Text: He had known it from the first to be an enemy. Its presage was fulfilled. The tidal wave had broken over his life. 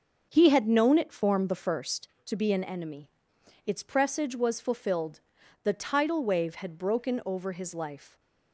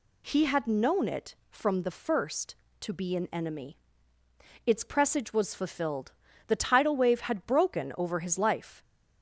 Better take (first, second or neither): second